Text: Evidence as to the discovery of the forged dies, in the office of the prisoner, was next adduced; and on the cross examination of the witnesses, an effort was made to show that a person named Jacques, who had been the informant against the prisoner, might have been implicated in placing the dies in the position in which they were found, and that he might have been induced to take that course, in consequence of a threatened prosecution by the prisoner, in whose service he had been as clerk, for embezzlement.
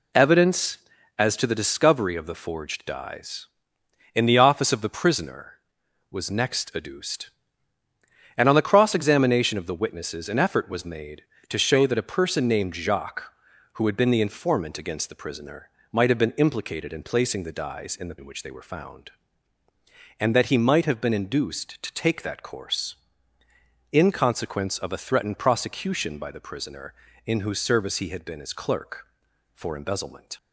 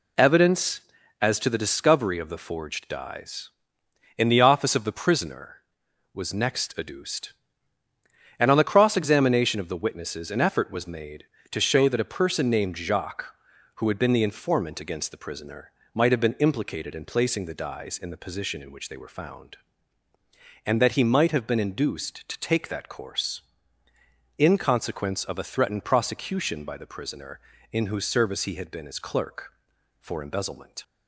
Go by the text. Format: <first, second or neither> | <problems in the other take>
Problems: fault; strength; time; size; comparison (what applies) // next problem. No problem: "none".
second | skips "position"; at 18.1 s